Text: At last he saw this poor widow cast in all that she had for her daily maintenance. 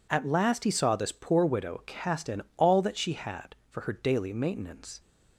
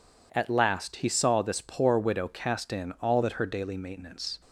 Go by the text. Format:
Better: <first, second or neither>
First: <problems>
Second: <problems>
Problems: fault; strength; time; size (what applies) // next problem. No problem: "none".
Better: first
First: none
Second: skips "she had for"; at 3.4 s